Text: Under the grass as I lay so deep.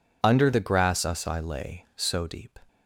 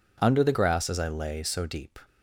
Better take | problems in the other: second | says "us" for "as"; at 1.0 s

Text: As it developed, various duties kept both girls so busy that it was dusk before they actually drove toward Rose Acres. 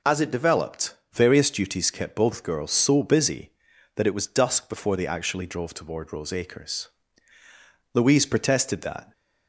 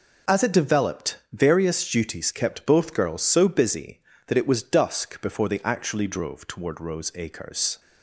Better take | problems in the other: second | goes on to say "Louise protested that"; noticeable; from 7.9 s on; 1.1 s long

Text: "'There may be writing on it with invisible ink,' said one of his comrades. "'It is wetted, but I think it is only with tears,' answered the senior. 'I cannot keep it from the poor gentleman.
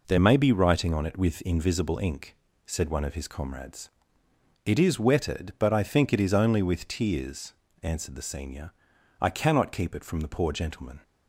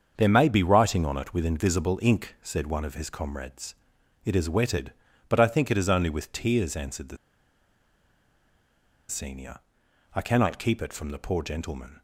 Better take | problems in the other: first | starts louder than the rest; until 1.1 s; 7 dB // pauses between "the" and "senior"; strong; at 7.1 s; 1.9 s long

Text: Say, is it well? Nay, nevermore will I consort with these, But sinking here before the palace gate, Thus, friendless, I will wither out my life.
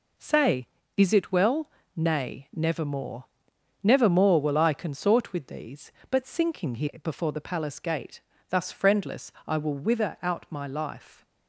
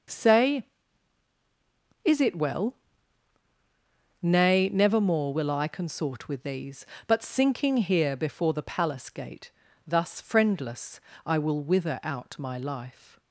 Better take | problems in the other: second | says "nevermore" twice; at 3.8 s

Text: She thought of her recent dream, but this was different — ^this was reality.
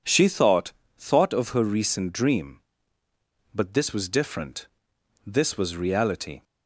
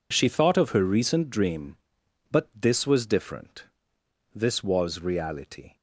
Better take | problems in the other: second | says "thought" twice; at 0.9 s

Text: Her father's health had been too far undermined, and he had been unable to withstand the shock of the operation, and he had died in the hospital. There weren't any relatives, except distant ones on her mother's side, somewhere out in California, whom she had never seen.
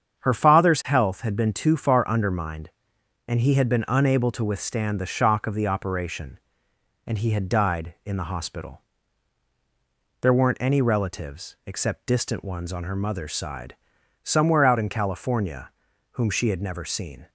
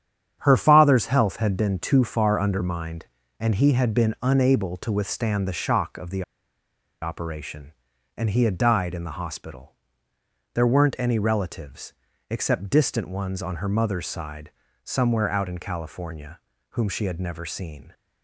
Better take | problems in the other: first | starts louder than the rest; strong; until 1.4 s; 8.5 dB; strong in the first // pauses between "the" and "operation"; noticeable; at 6.2 s; 0.78 s long

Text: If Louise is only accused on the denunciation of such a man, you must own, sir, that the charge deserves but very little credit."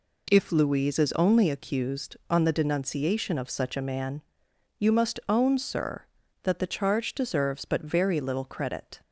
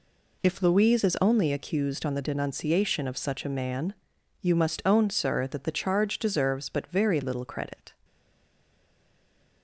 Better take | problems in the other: first | stays silent after the last word; noticeable; from 8.0 s on; 1.6 s long

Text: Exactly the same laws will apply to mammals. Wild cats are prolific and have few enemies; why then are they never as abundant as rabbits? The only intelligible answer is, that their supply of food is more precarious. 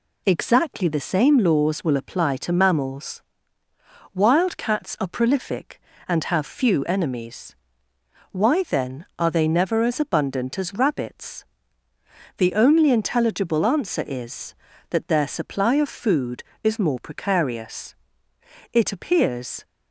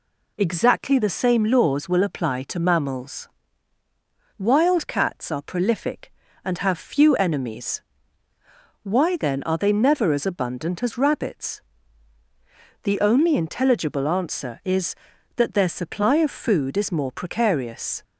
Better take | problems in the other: second | goes on to say "It appears"; noticeable; from 18.7 s on; 0.90 s long

